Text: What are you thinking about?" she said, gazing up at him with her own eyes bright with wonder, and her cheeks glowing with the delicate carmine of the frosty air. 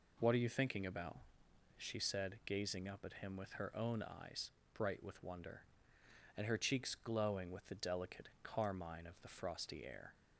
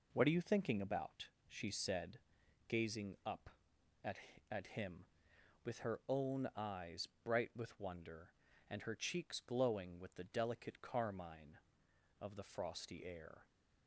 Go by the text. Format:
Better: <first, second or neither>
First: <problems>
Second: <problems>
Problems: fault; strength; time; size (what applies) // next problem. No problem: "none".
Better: first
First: pauses between "eyes" and "bright"; slight; at 4.4 s; 0.26 s long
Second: says "at" twice; at 4.5 s // pauses between "eyes" and "bright"; slight; at 7.0 s; 0.16 s long